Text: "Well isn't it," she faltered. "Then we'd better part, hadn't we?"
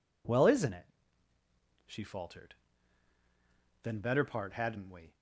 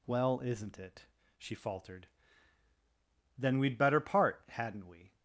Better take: second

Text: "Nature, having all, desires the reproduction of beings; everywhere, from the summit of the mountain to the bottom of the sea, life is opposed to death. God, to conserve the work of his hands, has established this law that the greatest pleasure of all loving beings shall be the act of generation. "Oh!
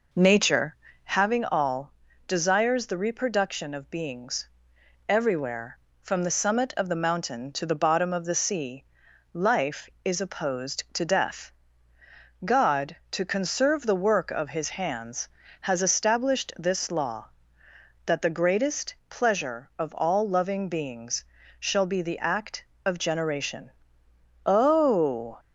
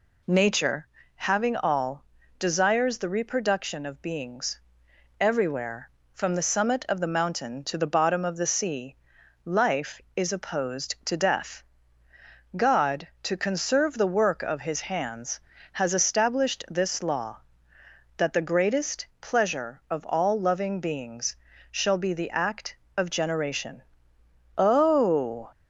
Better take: second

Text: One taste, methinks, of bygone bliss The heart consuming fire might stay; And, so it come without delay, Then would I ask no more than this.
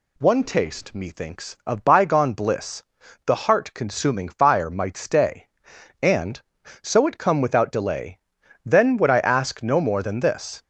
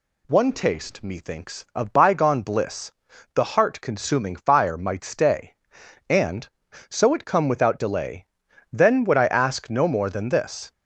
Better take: neither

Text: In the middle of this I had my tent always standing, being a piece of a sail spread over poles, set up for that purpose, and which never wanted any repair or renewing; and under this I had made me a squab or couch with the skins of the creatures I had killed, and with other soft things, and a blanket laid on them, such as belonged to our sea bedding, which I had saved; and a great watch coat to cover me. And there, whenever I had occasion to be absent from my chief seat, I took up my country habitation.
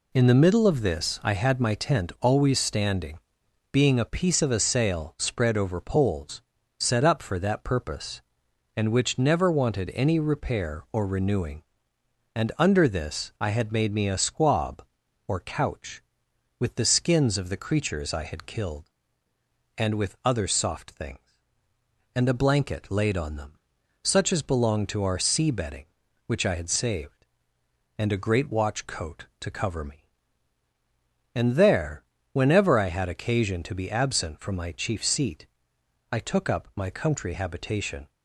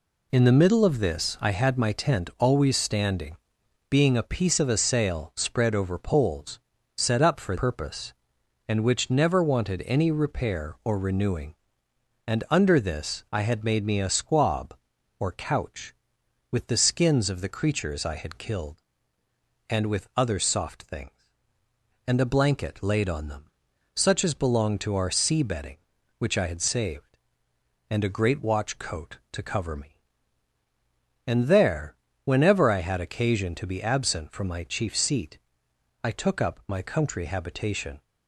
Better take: first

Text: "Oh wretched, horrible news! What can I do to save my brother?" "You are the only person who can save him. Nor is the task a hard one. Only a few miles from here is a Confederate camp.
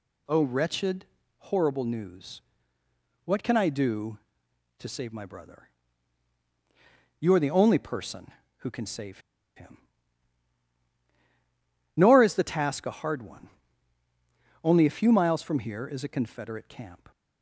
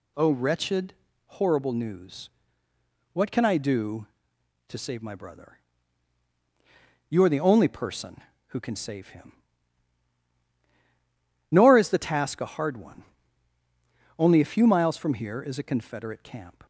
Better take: second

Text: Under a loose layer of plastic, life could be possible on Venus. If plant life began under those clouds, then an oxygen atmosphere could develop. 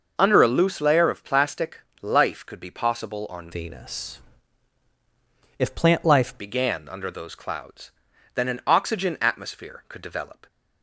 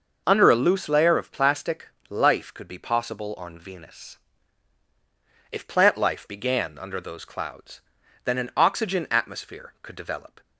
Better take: second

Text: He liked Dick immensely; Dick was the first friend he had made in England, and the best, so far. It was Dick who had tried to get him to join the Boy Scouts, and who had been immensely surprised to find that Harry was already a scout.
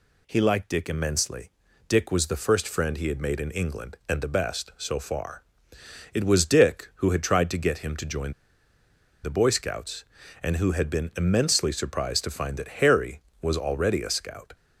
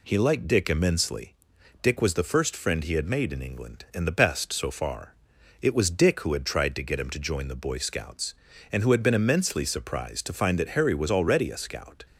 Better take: second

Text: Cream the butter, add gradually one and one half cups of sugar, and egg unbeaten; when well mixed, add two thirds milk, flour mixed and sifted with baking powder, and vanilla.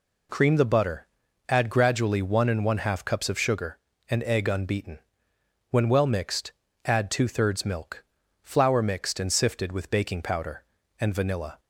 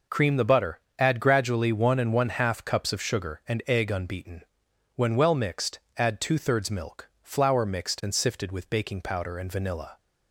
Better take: neither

